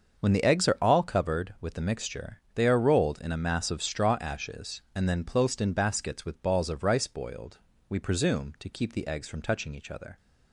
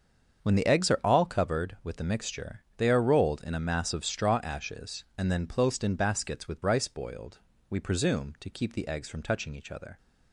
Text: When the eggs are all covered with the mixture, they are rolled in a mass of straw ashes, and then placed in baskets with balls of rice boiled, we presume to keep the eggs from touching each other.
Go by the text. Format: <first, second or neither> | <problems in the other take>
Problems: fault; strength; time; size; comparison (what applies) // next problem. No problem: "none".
first | starts louder than the rest; until 1.4 s; 7 dB; also in the first // skips "balls of"; at 6.6 s